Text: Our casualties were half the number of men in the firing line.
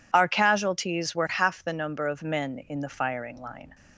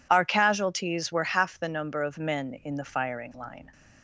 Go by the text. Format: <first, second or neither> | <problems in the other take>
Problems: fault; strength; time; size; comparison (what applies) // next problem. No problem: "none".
neither | none